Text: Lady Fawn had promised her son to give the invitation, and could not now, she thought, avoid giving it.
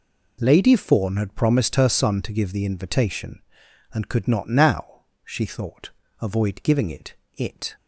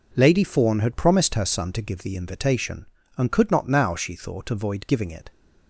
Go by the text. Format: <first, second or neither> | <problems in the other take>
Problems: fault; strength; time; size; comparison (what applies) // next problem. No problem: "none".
second | says "it" twice; at 7.3 s